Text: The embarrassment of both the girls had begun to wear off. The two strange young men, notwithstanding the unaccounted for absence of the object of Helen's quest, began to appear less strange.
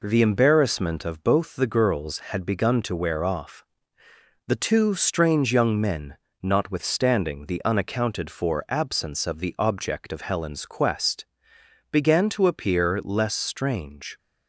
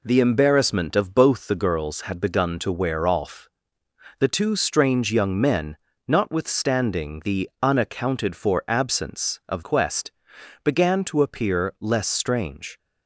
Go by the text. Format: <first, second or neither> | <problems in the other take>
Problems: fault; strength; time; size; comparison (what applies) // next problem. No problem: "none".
first | skips "the object of Helen's"; at 9.6 s